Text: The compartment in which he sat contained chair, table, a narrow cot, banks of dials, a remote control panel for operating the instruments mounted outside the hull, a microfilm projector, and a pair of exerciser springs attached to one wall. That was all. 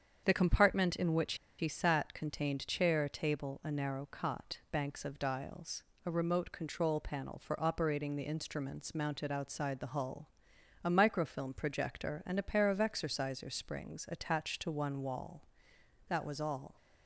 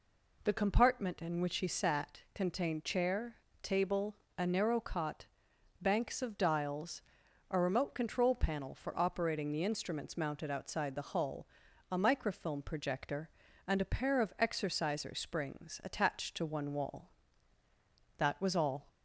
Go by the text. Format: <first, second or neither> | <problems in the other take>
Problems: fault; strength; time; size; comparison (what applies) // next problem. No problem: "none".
second | starts louder than the rest; strong; until 1.2 s; 7.5 dB // pauses between "which" and "he"; slight; at 1.3 s; 0.24 s long